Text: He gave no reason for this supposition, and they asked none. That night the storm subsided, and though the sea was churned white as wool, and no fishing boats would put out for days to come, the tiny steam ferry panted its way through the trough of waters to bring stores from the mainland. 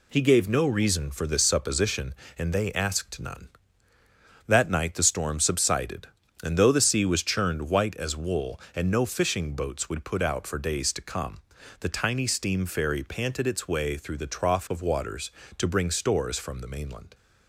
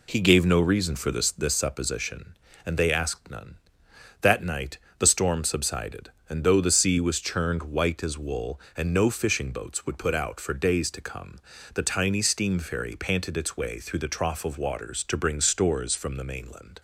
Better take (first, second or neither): first